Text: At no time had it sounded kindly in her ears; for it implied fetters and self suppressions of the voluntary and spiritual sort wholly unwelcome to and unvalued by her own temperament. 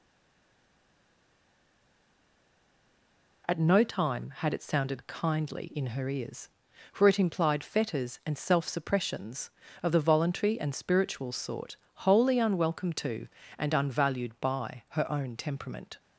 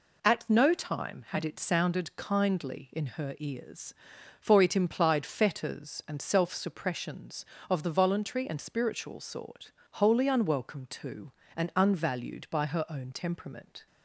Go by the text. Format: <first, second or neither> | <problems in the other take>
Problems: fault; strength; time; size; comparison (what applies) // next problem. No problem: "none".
second | stays silent before the first word; strong; until 3.4 s; 3.4 s long // pauses between "sort" and "wholly"; slight; at 11.7 s; 0.18 s long; slight in the second